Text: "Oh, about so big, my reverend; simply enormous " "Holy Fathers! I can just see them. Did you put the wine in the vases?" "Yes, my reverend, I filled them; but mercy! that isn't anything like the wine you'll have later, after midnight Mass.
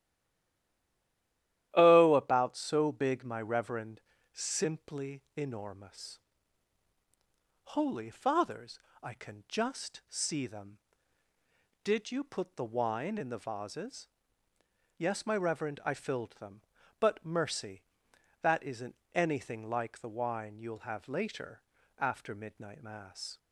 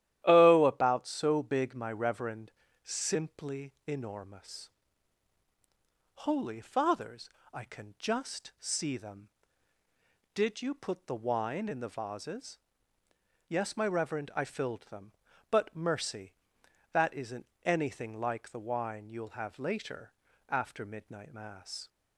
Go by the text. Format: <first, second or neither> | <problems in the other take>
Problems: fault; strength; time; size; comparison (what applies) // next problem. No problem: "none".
second | stays silent before the first word; noticeable; until 1.7 s; 1.7 s long // starts louder than the rest; strong; until 2.7 s; 13 dB; strong in the second // pauses between "simply" and "enormous"; slight; at 5.2 s; 0.16 s long; slight in the second // pauses between "isn't" and "anything"; slight; at 18.9 s; 0.18 s long; slight in the second